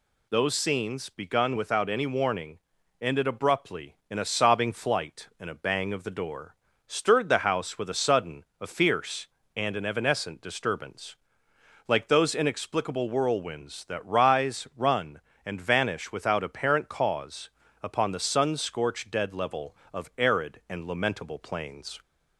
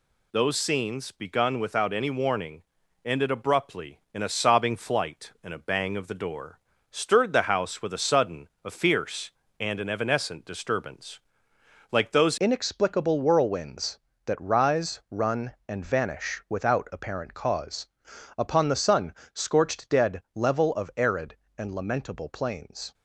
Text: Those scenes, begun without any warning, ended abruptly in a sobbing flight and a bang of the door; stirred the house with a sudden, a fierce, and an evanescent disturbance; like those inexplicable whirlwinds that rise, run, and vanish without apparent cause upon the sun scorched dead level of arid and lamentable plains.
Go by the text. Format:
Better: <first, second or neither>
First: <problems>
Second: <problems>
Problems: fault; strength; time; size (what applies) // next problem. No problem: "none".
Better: first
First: pauses between "cause" and "upon"; slight; at 17.4 s; 0.34 s long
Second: changes voice at "inexplicable"; from 12.3 s on; 10.6 s long // pauses between "cause" and "upon"; noticeable; at 17.8 s; 0.50 s long // pauses between "sun" and "scorched"; slight; at 19.1 s; 0.18 s long